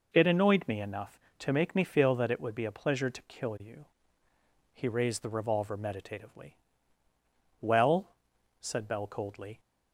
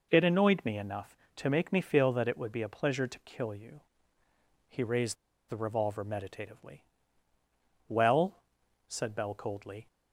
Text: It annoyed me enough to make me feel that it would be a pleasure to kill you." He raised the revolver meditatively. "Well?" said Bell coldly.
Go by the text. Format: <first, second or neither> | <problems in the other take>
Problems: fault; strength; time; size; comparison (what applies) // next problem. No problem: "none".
first | pauses between "raised" and "the"; slight; at 5.1 s; 0.35 s long